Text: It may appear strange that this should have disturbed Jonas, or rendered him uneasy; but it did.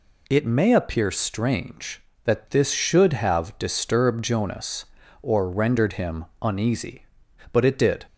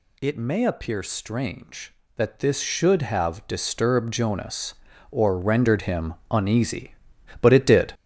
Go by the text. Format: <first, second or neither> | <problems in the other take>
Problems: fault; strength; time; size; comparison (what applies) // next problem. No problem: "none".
first | gets louder; throughout; 7 dB // pauses between "him" and "uneasy"; slight; at 6.1 s; 0.16 s long; slight in the first